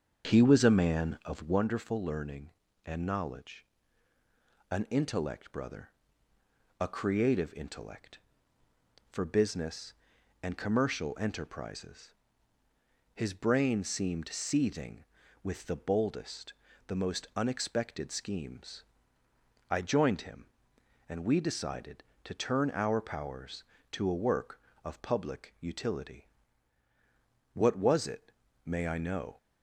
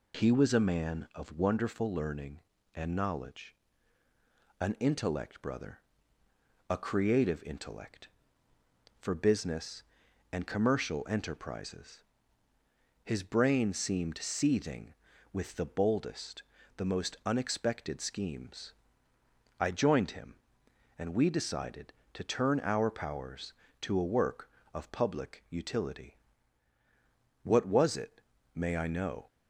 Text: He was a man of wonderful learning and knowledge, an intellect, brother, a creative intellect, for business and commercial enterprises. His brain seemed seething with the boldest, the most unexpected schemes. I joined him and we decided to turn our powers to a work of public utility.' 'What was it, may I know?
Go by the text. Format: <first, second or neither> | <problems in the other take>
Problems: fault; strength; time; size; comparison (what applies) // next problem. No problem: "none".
second | starts louder than the rest; strong; until 1.6 s; 7 dB